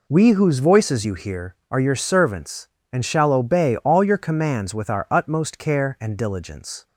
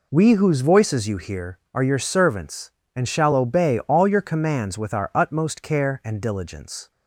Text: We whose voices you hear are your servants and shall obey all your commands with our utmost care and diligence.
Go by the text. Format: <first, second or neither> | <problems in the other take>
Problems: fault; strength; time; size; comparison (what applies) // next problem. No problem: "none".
neither | none